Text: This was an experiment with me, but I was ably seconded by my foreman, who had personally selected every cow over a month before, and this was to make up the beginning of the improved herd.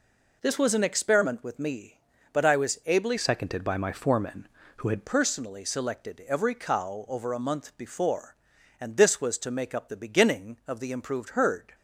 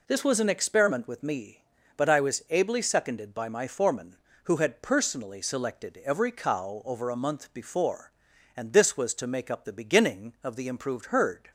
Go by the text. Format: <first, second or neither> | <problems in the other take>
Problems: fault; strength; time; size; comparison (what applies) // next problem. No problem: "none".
second | changes voice from "seconded" to "had"; from 3.1 to 5.0 s; 1.9 s long